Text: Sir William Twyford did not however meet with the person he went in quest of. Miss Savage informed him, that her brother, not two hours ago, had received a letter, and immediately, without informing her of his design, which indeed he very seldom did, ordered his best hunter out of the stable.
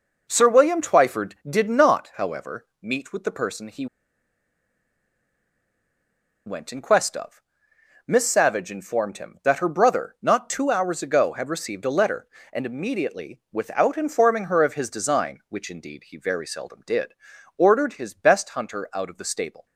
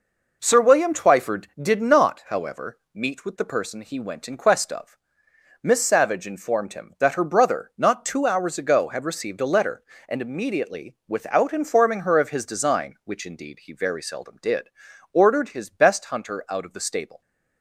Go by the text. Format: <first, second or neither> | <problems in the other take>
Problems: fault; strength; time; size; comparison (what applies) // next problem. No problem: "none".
second | pauses between "however" and "meet"; slight; at 2.6 s; 0.16 s long; slight in the second // pauses between "he" and "went"; strong; at 3.8 s; 2.6 s long